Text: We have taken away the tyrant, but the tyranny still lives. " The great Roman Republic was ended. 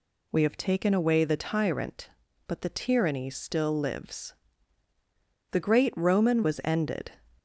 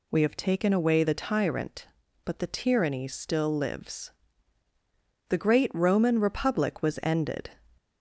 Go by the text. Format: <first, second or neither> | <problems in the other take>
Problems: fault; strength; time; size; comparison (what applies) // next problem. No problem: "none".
second | skips "Republic"; at 6.4 s